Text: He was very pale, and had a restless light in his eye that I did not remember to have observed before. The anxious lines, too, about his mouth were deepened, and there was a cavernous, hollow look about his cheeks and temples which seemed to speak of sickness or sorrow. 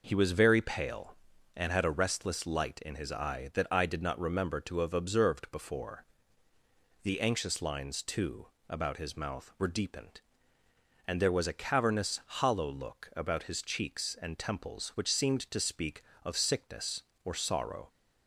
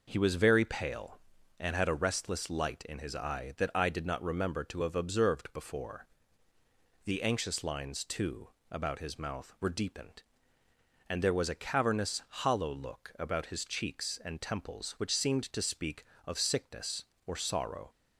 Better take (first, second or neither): neither